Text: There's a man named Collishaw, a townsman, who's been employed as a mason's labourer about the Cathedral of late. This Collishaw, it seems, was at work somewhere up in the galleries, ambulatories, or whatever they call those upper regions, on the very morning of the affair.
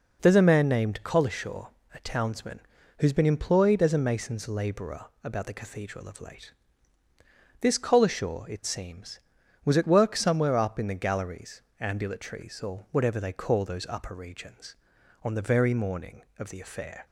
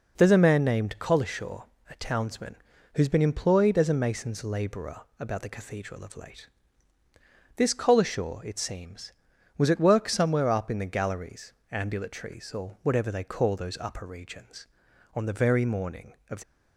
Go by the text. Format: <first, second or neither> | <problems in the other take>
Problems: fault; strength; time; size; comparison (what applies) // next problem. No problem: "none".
first | pauses between "labourer" and "about"; slight; at 5.0 s; 0.18 s long; slight in the first // stops before "the affair"; at 16.4 s